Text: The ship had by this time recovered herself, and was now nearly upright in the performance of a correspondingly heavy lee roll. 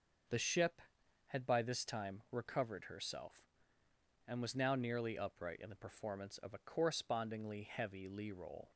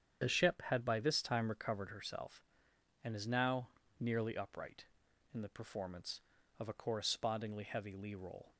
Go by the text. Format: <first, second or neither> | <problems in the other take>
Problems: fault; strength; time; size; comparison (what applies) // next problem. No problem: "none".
first | starts louder than the rest; strong; until 1.2 s; 8 dB; also in the first // says "is" for "was"; at 3.1 s // pauses between "now" and "nearly"; slight; at 3.7 s; 0.28 s long